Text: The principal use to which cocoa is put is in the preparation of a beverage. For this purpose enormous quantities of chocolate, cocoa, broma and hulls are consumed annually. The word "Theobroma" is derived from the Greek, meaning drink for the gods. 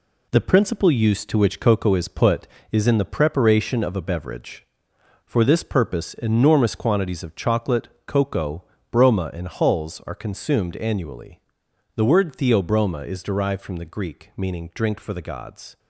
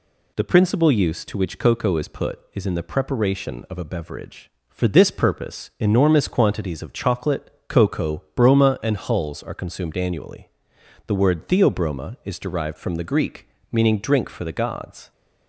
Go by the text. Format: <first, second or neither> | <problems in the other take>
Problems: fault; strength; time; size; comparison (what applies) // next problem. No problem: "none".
second | gets quieter; throughout; 6.5 dB